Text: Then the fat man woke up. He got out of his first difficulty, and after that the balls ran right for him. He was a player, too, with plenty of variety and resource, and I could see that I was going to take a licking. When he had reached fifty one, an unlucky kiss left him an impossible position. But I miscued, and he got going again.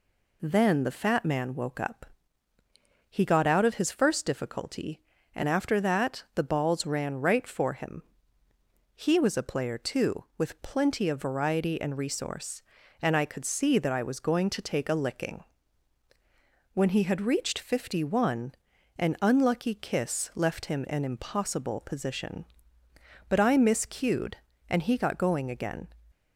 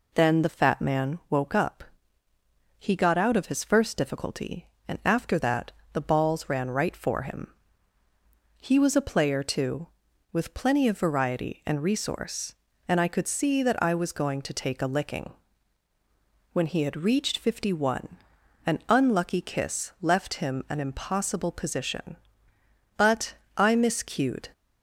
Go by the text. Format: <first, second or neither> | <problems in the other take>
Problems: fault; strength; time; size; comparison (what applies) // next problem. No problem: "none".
first | pauses between "that" and "the"; slight; at 5.7 s; 0.20 s long // pauses between "But" and "I"; slight; at 23.3 s; 0.22 s long // stops before "and he got going again"; at 24.5 s